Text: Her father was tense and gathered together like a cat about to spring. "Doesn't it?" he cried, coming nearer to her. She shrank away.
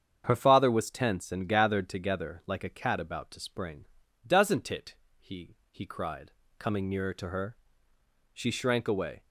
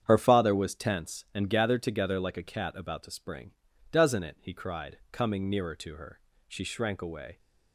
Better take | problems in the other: second | starts louder than the rest; strong; until 1.2 s; 7.5 dB; strong in the second // says "he" twice; at 5.7 s

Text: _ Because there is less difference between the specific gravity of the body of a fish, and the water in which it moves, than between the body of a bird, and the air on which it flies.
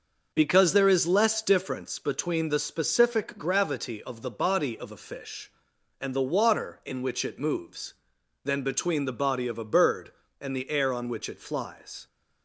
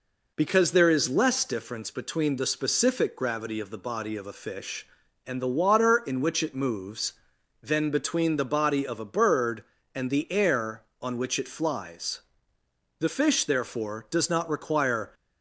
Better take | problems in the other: first | goes on to say "The fish therefore does not require"; strong; from 12.9 s on; 2.1 s long

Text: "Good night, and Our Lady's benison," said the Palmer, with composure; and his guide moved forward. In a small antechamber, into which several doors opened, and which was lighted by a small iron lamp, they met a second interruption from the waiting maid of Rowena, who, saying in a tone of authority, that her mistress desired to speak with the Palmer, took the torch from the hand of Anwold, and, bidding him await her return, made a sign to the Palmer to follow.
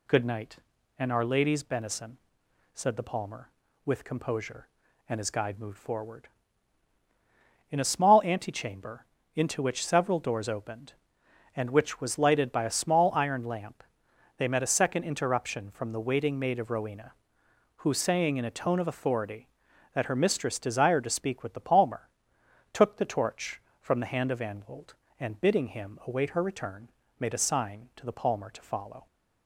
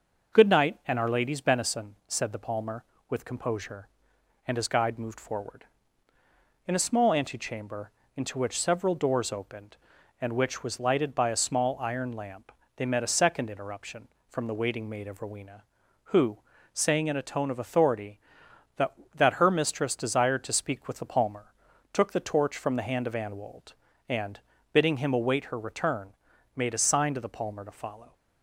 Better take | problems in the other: first | says "that" twice; at 19.1 s

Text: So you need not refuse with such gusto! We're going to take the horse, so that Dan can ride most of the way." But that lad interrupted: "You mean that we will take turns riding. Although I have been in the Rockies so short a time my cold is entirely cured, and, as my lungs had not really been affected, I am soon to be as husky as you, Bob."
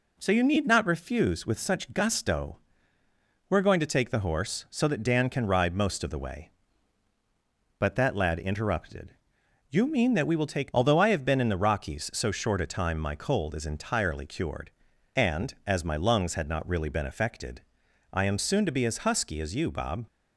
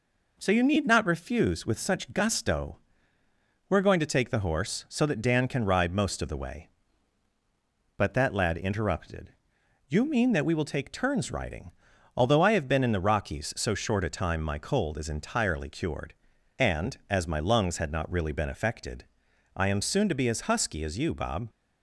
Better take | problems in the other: second | skips "turns riding"; at 10.7 s

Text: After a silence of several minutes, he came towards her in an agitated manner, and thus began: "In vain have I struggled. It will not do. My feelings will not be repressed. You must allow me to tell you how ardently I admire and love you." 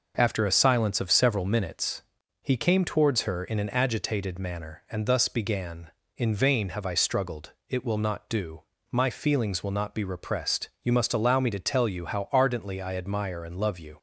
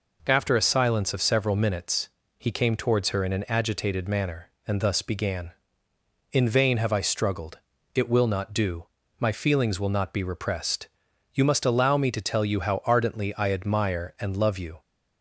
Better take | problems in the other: neither | none

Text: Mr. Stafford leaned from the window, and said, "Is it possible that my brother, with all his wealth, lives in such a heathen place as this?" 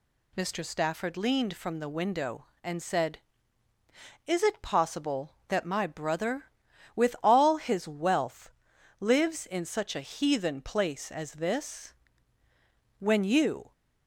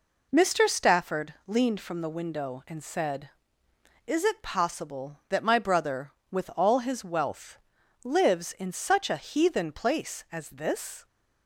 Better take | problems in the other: second | goes on to say "When you"; noticeable; from 12.9 s on; 0.76 s long

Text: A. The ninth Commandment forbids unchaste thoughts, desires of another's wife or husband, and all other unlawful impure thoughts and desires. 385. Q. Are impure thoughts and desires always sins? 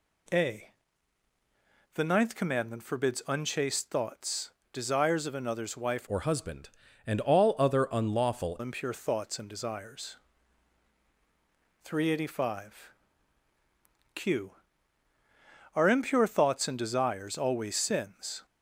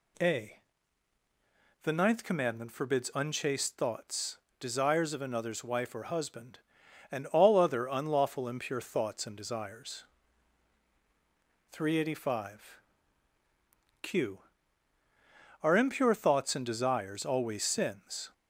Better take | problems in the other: second | changes voice from "or" to "unlawful"; from 6.0 to 8.5 s; 2.5 s long

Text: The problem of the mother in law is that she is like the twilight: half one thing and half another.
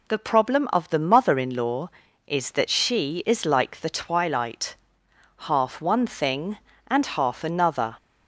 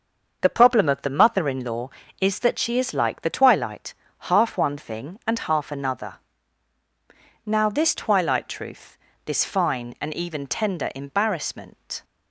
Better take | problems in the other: first | starts louder than the rest; until 1.4 s; 6.5 dB // goes on to say "Now this twilight truth this fine and even tender embarrassment"; strong; from 7.4 s on; 4.6 s long

